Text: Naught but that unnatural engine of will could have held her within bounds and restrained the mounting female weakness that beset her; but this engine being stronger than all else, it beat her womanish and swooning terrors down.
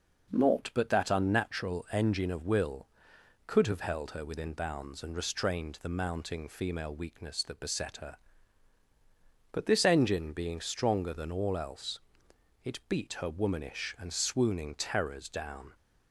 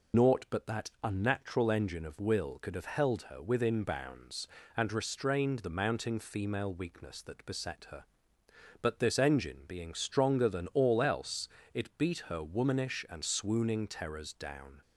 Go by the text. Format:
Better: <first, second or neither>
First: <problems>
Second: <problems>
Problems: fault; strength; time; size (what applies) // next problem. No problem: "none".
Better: first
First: none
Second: loses the start of "Naught"; at 0.1 s; 75 ms